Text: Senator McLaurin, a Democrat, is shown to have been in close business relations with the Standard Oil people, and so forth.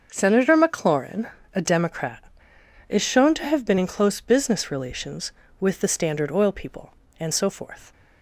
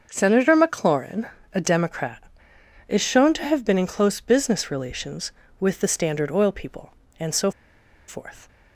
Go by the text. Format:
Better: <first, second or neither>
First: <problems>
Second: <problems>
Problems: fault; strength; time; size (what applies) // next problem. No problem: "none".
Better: first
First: starts louder than the rest; until 1.1 s; 6.5 dB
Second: starts louder than the rest; until 1.1 s; 6.5 dB // pauses between "so" and "forth"; noticeable; at 7.5 s; 0.57 s long